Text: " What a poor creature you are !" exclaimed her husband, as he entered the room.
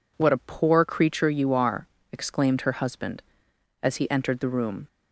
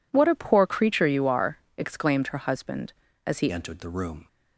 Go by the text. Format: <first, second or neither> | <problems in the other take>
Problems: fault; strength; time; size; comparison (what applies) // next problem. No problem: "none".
first | changes voice at "entered"; from 3.5 s on; 0.7 s long